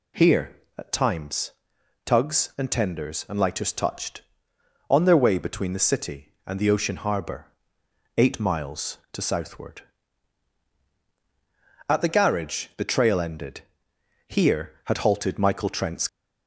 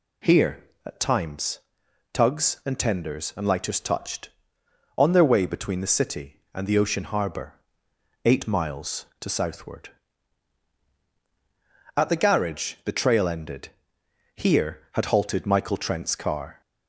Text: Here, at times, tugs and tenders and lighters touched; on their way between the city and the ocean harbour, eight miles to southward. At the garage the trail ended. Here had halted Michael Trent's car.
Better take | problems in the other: second | stops before "car"; at 16.0 s

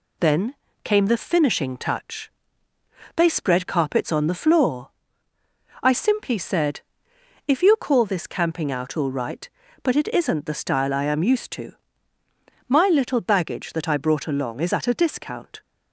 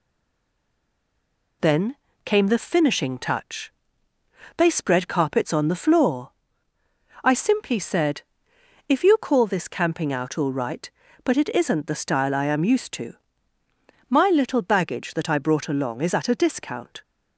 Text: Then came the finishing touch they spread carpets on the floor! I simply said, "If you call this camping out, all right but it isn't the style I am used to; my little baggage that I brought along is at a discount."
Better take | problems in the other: first | stays silent before the first word; noticeable; until 1.6 s; 1.6 s long // pauses between "Then" and "came"; slight; at 1.9 s; 0.30 s long; slight in the first // pauses between "touch" and "they"; noticeable; at 3.7 s; 0.86 s long; noticeable in the first

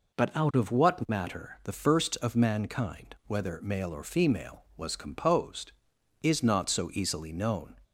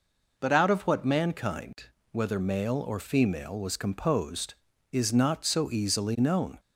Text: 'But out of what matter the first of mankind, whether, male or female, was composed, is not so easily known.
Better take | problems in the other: first | skips "matter the first of"; at 1.0 s

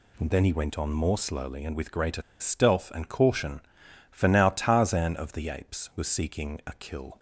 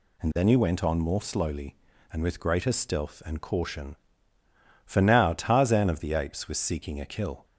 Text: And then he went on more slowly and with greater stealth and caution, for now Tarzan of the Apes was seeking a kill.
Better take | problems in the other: second | pauses between "greater" and "stealth"; slight; at 2.2 s; 0.19 s long

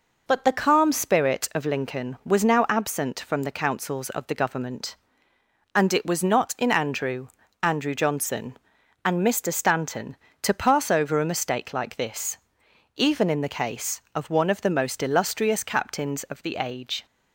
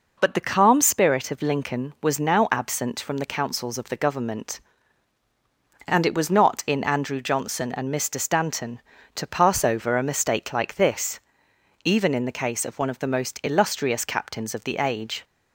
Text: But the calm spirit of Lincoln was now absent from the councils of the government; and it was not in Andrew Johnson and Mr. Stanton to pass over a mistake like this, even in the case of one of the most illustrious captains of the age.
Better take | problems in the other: second | says "Andrew" twice; at 7.6 s

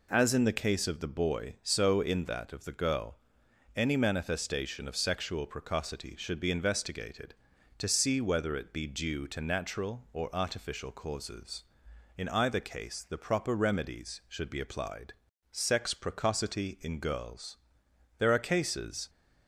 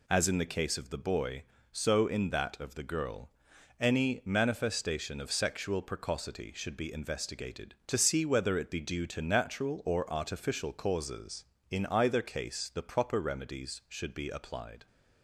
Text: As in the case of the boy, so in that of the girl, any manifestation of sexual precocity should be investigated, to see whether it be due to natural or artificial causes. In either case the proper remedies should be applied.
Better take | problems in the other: second | goes on to say "SEX PRECOCITY IN GIRLS There are cases"; strong; from 15.5 s on; 3.5 s long

